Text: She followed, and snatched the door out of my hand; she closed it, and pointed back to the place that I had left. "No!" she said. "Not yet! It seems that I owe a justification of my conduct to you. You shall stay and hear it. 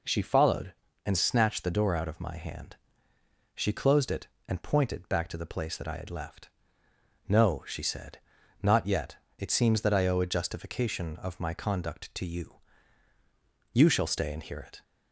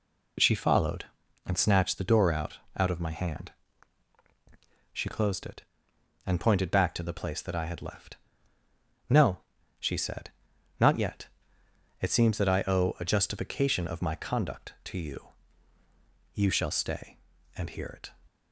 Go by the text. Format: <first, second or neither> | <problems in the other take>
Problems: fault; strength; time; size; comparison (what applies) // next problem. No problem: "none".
first | says "out" twice; at 2.7 s